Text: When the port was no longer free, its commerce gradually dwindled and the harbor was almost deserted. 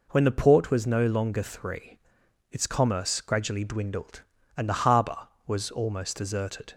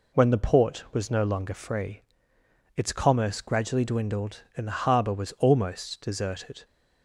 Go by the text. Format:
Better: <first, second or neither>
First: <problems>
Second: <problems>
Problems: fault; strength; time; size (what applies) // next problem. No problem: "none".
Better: second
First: says "three" for "free"; at 1.4 s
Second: none